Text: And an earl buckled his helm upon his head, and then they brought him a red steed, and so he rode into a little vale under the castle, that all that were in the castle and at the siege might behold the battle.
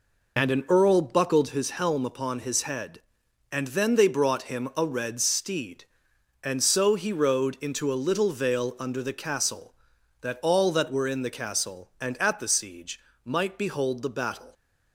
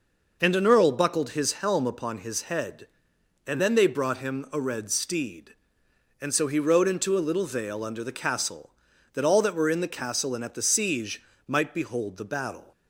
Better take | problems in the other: neither | pauses between "siege" and "might"; slight; the same in both

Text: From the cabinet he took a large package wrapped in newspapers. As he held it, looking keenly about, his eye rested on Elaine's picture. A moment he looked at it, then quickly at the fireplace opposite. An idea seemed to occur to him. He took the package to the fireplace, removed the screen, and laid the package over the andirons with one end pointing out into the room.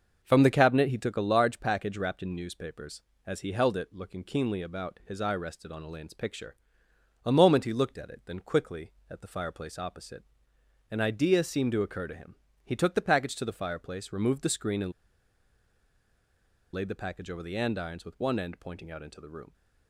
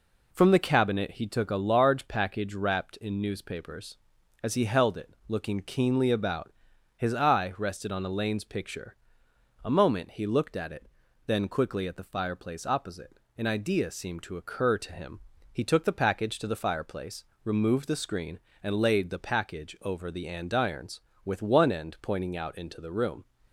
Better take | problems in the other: second | starts louder than the rest; until 1.2 s; 6 dB // pauses between "and" and "laid"; strong; at 14.9 s; 1.8 s long

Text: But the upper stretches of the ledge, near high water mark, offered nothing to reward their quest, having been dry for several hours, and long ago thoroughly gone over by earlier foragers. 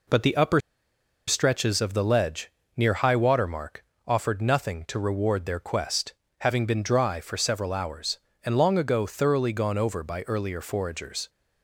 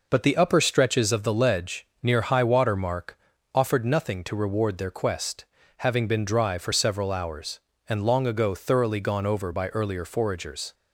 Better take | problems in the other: second | pauses between "upper" and "stretches"; noticeable; at 0.5 s; 0.69 s long

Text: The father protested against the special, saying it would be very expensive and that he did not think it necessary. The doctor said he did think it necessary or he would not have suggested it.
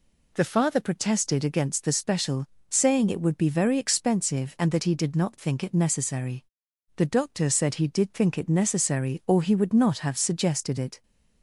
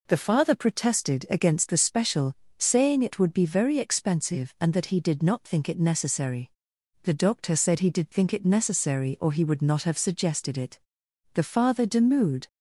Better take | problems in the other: first | goes on to say "The father demurred"; noticeable; from 11.3 s on; 1.1 s long

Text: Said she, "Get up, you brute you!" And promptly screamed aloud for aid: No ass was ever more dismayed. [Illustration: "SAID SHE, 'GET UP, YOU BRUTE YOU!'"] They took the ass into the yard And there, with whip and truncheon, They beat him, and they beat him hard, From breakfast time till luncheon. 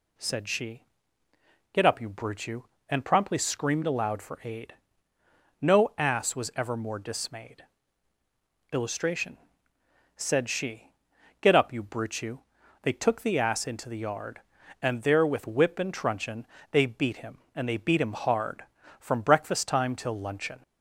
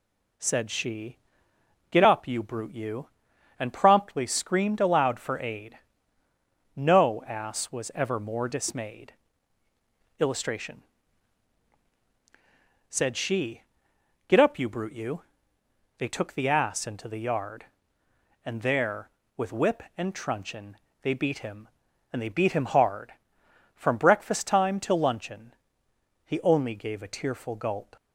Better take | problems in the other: first | goes on to say "He only gave a tearful gulp"; strong; from 26.2 s on; 1.7 s long

